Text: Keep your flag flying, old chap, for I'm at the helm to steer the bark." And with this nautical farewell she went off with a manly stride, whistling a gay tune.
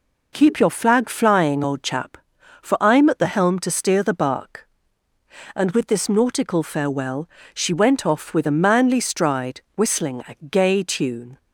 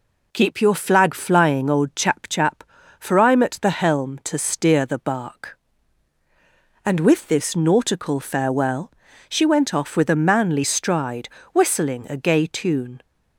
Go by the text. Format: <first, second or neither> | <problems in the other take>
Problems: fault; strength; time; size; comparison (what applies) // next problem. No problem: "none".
first | says "chap" twice; at 2.2 s // pauses between "farewell" and "she"; at 8.9 s; 0.38 s long; slight in the first